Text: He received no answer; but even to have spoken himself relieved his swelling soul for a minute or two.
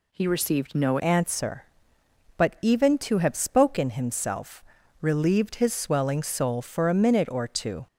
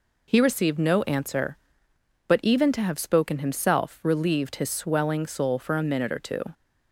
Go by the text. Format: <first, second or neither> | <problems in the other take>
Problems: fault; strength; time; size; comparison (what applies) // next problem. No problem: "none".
second | changes voice at "answer"; from 1.0 s on; 6.8 s long // pauses between "himself" and "relieved"; at 4.6 s; 0.40 s long